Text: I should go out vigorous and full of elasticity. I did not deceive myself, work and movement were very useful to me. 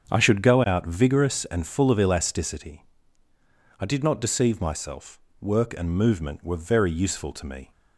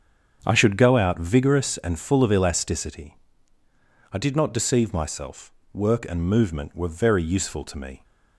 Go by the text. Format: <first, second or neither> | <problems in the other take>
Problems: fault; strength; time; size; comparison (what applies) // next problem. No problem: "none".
neither | starts louder than the rest; strong; the same in both